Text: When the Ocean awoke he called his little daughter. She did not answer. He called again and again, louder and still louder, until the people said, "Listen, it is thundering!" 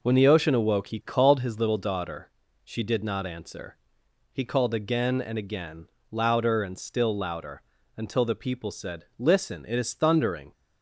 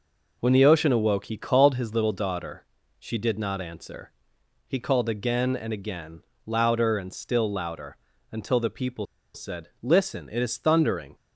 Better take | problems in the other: first | pauses between "people" and "said"; slight; at 9.0 s; 0.29 s long

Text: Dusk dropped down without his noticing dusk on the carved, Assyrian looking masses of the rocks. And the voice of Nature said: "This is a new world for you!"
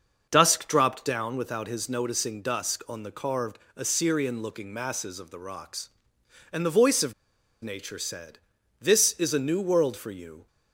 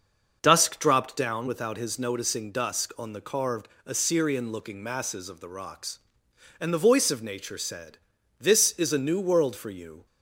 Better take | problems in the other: second | starts louder than the rest; until 1.3 s; 6 dB; also in the second // pauses between "of" and "Nature"; noticeable; at 7.1 s; 0.48 s long

